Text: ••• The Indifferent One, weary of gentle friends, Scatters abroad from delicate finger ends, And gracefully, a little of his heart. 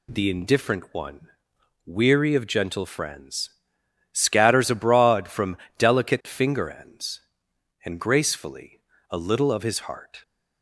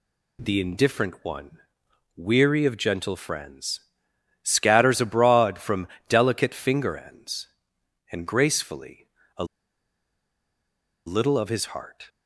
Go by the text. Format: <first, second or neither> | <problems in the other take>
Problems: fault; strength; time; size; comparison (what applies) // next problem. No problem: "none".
first | pauses between "from" and "delicate"; slight; at 5.8 s; 0.22 s long; slight in the first // pauses between "a" and "little"; strong; at 9.4 s; 1.6 s long